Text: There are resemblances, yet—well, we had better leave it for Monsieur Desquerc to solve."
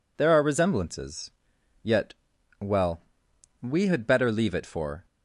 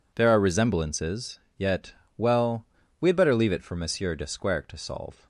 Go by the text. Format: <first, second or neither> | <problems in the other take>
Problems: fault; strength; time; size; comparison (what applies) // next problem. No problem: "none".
second | stops before "Monsieur Desquerc to solve"; at 5.0 s